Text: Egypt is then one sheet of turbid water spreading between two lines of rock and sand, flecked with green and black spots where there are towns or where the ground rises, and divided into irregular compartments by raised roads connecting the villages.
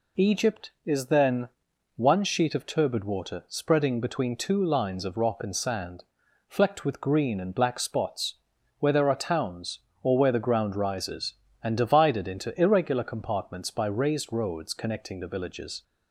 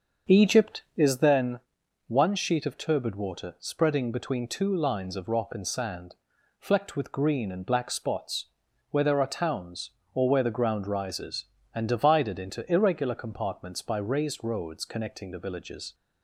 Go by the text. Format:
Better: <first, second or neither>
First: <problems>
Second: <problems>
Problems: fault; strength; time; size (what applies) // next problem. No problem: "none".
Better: first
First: pauses between "then" and "one"; noticeable; at 1.4 s; 0.48 s long // pauses between "spots" and "where"; at 8.3 s; 0.44 s long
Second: starts louder than the rest; until 1.3 s; 6.5 dB // pauses between "then" and "one"; noticeable; at 1.5 s; 0.48 s long // pauses between "spots" and "where"; at 8.4 s; 0.44 s long